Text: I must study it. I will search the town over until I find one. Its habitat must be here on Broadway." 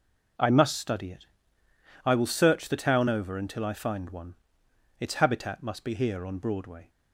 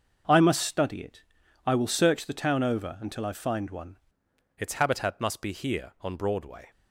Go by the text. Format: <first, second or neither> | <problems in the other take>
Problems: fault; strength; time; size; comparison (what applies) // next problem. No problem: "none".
first | starts louder than the rest; until 1.7 s; 6.5 dB // changes voice at "Its"; from 4.5 s on; 2.2 s long